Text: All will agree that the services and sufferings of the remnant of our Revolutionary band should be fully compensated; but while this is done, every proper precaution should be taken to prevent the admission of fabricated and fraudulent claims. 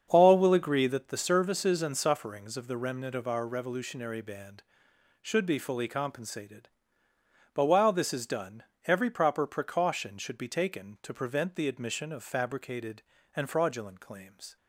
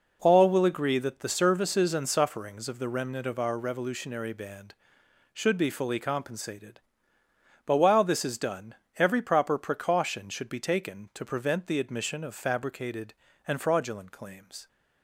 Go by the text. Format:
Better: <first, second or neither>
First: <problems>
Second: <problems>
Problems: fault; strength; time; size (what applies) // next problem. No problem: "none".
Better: second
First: starts louder than the rest; strong; until 1.1 s; 7.5 dB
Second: none